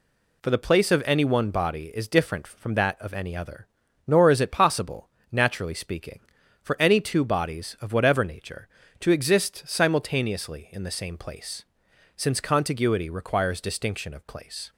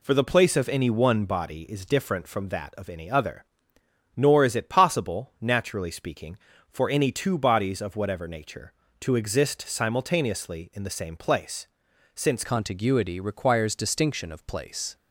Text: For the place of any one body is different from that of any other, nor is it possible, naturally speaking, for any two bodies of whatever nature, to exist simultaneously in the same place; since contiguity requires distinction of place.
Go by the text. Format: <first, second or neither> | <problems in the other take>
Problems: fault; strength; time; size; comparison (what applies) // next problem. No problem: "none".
first | changes voice at "contiguity"; from 12.4 s on; 2.5 s long